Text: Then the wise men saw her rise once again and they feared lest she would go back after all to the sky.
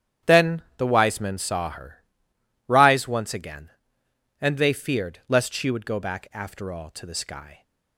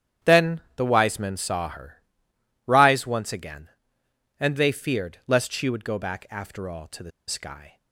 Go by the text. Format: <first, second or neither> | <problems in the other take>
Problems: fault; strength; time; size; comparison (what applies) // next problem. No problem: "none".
first | starts louder than the rest; strong; until 1.4 s; 9.5 dB; strong in the first // pauses between "Then" and "the"; slight; at 0.5 s; 0.16 s long; slight in the first // pauses between "her" and "rise"; noticeable; at 2.0 s; 0.64 s long; noticeable in the first // pauses between "the" and "sky"; slight; at 7.1 s; 0.17 s long